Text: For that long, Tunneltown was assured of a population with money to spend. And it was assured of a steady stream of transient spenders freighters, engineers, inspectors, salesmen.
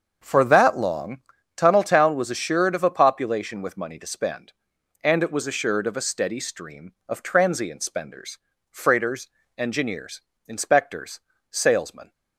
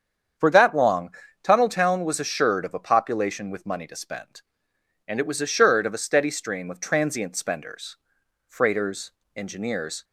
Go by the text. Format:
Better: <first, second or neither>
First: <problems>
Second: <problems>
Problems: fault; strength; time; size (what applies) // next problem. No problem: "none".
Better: first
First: starts louder than the rest; until 1.6 s; 6.5 dB // pauses between "spenders" and "freighters"; slight; at 8.3 s; 0.32 s long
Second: starts louder than the rest; strong; until 1.7 s; 8 dB // pauses between "spenders" and "freighters"; noticeable; at 7.9 s; 0.52 s long // stops before "inspectors salesmen"; at 10.0 s